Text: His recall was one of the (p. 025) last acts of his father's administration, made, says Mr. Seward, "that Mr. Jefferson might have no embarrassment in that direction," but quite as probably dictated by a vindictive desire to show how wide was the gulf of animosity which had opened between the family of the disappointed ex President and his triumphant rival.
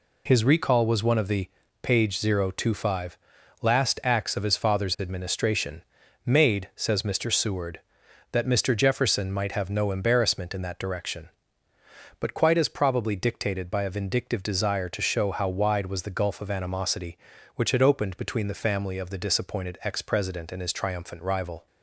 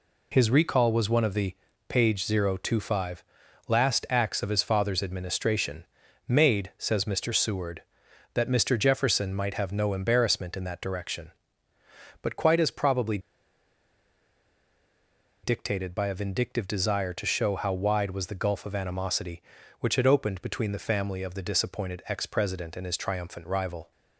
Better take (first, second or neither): first